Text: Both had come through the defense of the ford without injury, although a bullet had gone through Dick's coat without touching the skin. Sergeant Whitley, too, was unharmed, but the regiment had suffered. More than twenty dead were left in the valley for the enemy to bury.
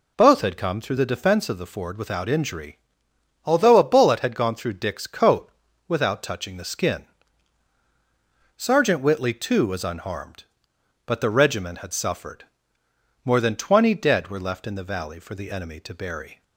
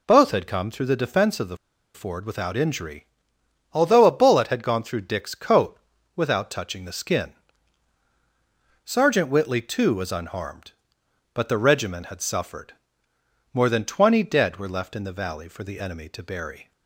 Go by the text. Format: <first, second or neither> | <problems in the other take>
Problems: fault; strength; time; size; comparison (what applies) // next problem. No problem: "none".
first | pauses between "the" and "ford"; at 1.5 s; 0.38 s long // pauses between "coat" and "without"; at 5.7 s; 0.38 s long; also in the first